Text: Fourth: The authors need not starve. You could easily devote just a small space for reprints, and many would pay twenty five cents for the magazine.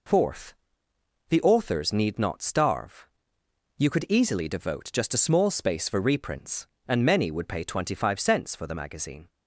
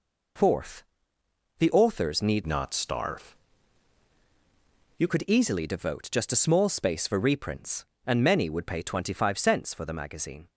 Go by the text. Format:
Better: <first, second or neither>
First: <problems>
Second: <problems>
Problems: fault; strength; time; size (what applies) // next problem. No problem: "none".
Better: first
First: none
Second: changes voice from "not" to "You"; from 2.4 to 5.0 s; 2.6 s long